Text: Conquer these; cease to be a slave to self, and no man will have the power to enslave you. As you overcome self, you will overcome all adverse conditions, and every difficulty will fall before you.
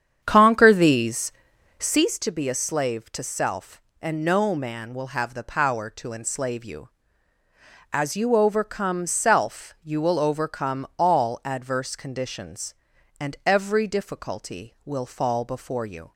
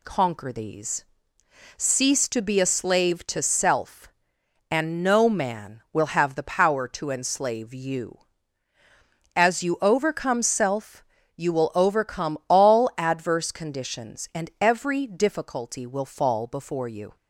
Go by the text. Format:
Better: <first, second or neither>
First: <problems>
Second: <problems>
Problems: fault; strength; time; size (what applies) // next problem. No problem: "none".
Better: second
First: starts louder than the rest; strong; until 2.1 s; 8.5 dB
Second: none